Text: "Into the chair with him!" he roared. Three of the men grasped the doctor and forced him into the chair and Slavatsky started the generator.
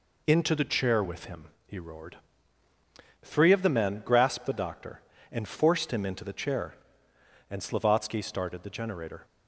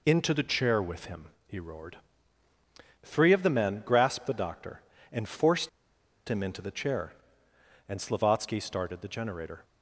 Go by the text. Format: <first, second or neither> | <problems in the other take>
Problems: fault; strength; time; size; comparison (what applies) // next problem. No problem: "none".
first | pauses between "forced" and "him"; noticeable; at 5.6 s; 0.59 s long